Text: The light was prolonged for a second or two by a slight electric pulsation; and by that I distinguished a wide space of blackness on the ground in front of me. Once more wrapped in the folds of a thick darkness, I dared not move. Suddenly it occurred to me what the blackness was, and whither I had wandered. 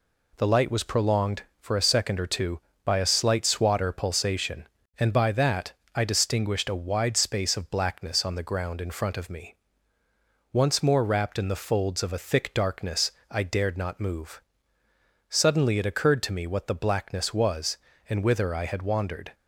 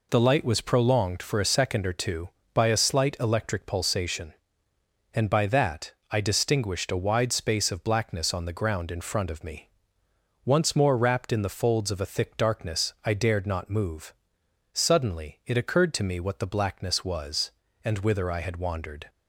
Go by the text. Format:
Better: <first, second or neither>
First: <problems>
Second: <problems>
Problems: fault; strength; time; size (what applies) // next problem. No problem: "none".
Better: second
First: says "swatter" for "electric"; at 3.4 s // pauses between "that" and "I"; slight; at 5.7 s; 0.20 s long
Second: pauses between "that" and "I"; slight; at 5.9 s; 0.18 s long